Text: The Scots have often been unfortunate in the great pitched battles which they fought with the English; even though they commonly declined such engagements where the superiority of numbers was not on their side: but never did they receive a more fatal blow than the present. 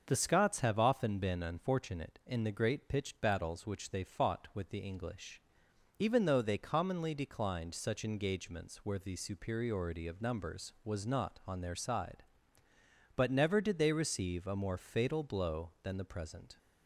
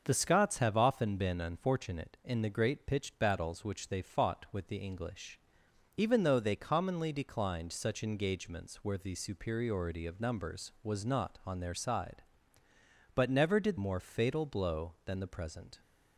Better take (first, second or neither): first